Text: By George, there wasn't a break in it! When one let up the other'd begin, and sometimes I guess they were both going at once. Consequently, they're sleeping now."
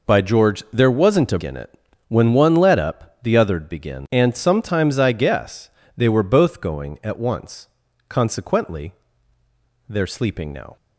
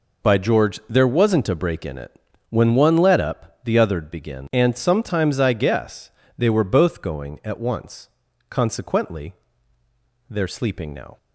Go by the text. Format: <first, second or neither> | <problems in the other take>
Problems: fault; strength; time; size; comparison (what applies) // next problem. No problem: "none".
second | skips "break"; at 1.4 s // pauses between "guess" and "they"; slight; at 5.6 s; 0.26 s long; slight in the second